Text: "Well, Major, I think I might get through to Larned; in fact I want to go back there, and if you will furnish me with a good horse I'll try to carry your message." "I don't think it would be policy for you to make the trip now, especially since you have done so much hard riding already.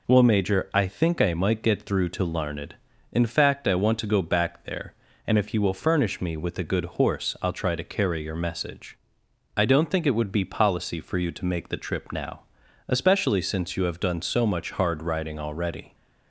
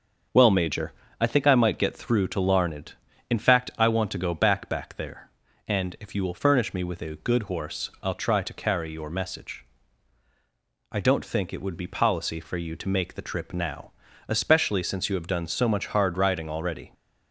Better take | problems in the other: first | starts louder than the rest; until 1.5 s; 6.5 dB // says "back" twice; at 4.6 s

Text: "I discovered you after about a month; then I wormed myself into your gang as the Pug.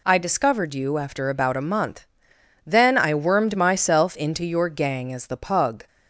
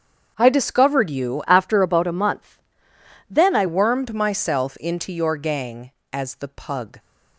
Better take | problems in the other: first | starts louder than the rest; strong; until 1.3 s; 7.5 dB // changes voice from "after" to "I"; from 1.4 to 3.6 s; 2.2 s long

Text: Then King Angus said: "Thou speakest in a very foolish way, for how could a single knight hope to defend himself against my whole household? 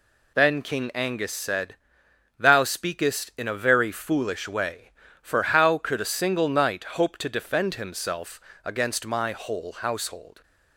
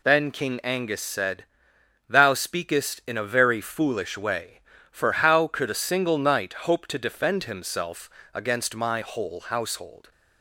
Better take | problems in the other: neither | pauses between "himself" and "against"; slight; the same in both

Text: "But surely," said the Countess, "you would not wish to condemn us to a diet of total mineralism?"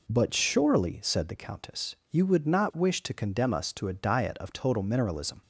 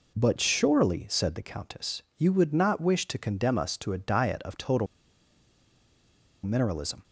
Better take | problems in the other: first | pauses between "total" and "mineralism"; strong; at 4.8 s; 1.5 s long

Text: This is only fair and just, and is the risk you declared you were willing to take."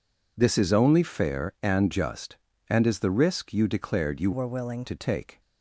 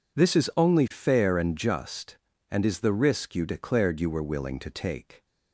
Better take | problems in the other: second | changes voice from "were" to "willing"; from 4.3 to 4.8 s; 0.5 s long

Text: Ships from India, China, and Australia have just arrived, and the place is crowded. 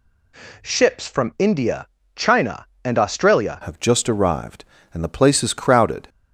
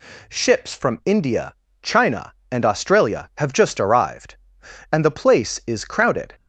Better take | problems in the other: second | changes voice at "have"; from 3.6 s on; 2.4 s long

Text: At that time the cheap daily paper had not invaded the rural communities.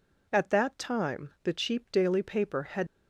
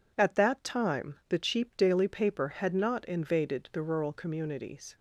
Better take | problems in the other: second | stops before "not invaded the rural communities"; at 2.8 s

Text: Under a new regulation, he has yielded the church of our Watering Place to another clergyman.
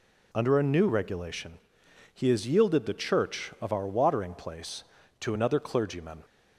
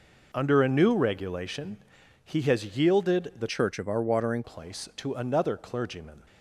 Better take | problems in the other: first | changes voice from "church" to "Watering"; from 3.5 to 4.4 s; 0.9 s long

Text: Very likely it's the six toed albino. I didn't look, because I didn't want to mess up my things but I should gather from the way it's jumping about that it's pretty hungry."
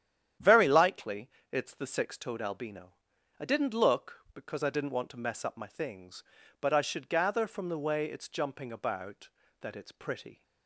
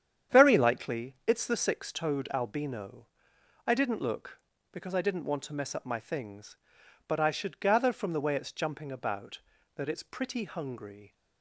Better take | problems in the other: second | starts louder than the rest; strong; until 1.6 s; 10 dB; strong in the second // pauses between "likely" and "it's"; slight; at 1.3 s; 0.20 s long // stops before "hungry"; at 10.4 s

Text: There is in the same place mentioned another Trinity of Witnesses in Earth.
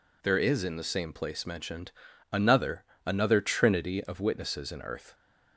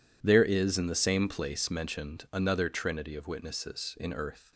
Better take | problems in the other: second | pauses between "mentioned" and "another"; at 1.9 s; 0.40 s long // says "another" twice; at 3.0 s

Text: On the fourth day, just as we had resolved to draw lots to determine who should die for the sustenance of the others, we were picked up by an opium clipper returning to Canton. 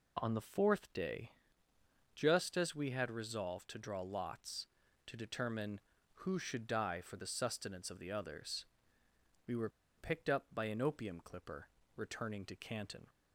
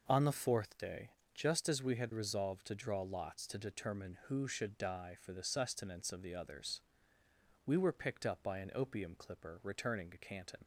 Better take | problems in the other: second | pauses between "were" and "picked"; slight; at 9.6 s; 0.27 s long // pauses between "clipper" and "returning"; slight; at 11.6 s; 0.28 s long

